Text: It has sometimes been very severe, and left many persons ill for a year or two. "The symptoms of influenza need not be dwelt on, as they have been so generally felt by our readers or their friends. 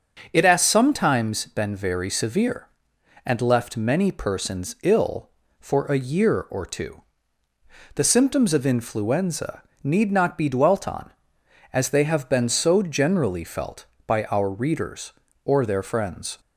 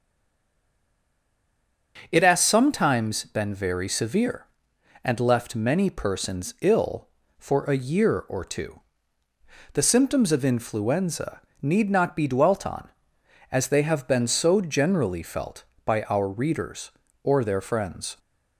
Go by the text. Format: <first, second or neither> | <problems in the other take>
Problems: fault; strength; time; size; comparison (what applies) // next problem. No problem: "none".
first | stays silent before the first word; noticeable; until 1.9 s; 1.9 s long // starts louder than the rest; until 3.1 s; 6.5 dB; also in the first // pauses between "influenza" and "need"; slight; at 11.4 s; 0.22 s long; slight in the first